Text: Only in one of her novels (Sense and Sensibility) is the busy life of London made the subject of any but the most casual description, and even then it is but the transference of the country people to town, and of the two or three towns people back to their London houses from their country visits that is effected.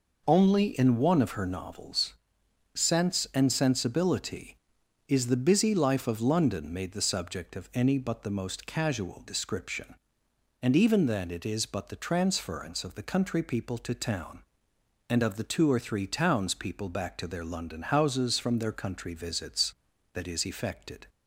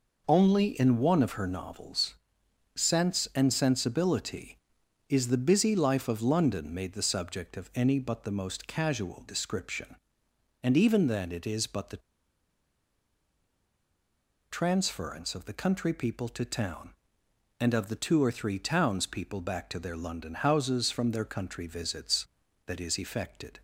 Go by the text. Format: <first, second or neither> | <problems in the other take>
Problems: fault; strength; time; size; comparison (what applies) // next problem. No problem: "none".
first | pauses between "the" and "transference"; strong; at 11.9 s; 2.5 s long